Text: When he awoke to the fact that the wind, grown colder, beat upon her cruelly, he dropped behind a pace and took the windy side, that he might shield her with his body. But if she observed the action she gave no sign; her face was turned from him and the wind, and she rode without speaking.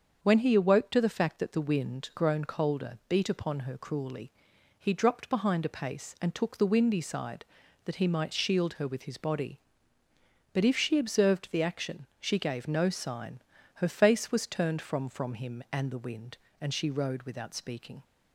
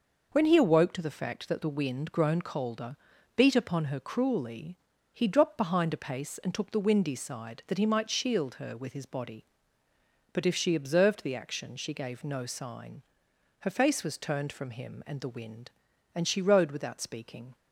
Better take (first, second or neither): second